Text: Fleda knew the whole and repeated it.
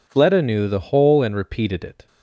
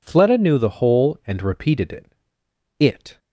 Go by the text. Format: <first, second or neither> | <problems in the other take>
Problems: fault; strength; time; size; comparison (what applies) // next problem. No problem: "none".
first | says "it" twice; at 2.8 s